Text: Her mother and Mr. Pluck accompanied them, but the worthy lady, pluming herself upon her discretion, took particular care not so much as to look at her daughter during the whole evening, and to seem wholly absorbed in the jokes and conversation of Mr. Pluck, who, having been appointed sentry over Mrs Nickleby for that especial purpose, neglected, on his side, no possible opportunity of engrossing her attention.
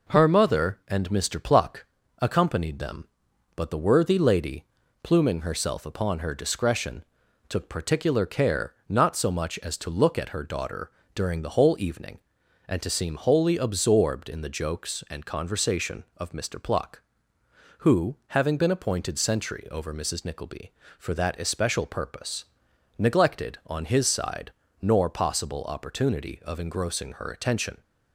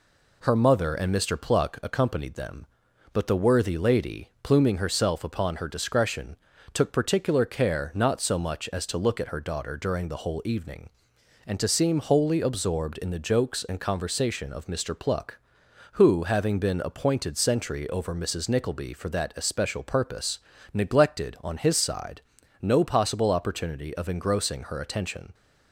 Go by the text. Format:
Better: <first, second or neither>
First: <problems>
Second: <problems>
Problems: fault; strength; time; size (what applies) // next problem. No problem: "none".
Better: second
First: pauses between "Pluck" and "accompanied"; slight; at 1.8 s; 0.36 s long // pauses between "daughter" and "during"; slight; at 10.8 s; 0.24 s long // says "nor" for "no"; at 24.7 s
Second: none